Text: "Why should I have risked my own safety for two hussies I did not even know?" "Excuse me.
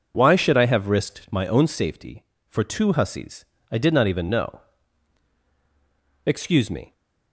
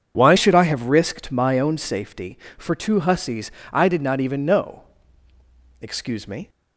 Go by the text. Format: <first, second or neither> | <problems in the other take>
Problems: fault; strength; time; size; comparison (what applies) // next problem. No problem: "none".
first | changes voice at "should"; from 0.3 s on; 6.1 s long // pauses between "hussies" and "I"; slight; at 3.5 s; 0.20 s long; slight in the first